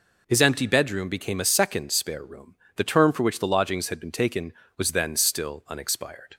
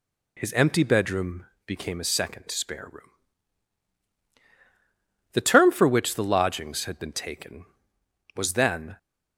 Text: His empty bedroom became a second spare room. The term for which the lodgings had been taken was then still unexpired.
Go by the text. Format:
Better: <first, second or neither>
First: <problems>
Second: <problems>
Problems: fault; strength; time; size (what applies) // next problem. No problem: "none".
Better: first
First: none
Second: pauses between "bedroom" and "became"; slight; at 1.4 s; 0.20 s long // stops before "still unexpired"; at 8.9 s